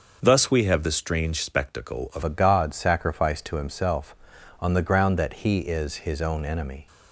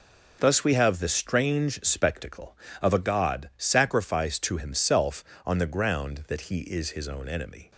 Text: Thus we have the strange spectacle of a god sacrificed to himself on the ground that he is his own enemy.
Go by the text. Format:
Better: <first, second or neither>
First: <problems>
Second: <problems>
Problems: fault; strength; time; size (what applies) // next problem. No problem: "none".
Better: second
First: starts louder than the rest; noticeable; until 1.2 s; 6 dB // changes voice at "a"; from 2.2 s on; 4.6 s long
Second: none